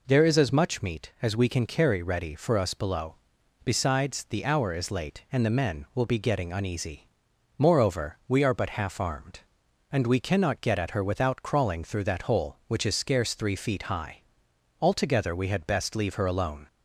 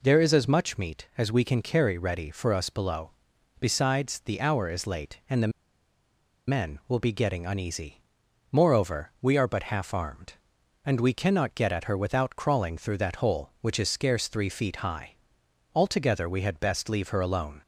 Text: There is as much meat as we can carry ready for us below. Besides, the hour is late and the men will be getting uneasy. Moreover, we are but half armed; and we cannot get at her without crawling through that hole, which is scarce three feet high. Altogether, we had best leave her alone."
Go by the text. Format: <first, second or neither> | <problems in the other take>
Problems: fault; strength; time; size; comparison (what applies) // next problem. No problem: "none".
first | pauses between "the" and "men"; at 5.5 s; 0.98 s long